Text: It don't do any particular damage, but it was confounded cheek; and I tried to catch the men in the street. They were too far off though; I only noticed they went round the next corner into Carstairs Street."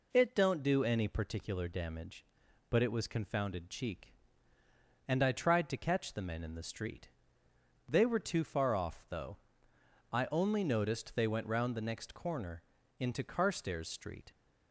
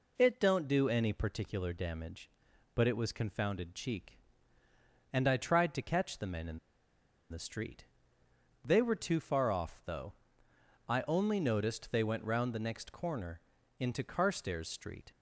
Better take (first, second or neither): first